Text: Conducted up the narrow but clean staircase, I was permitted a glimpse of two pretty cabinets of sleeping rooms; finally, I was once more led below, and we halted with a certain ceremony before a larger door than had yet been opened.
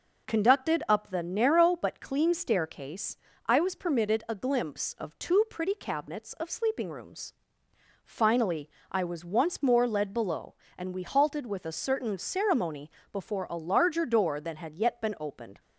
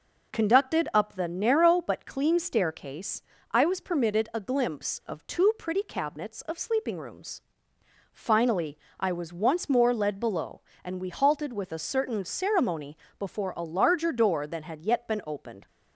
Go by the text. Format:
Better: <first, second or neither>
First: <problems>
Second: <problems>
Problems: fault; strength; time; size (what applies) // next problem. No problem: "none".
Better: neither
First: pauses between "ceremony" and "before"; slight; at 12.8 s; 0.20 s long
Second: pauses between "ceremony" and "before"; slight; at 12.9 s; 0.20 s long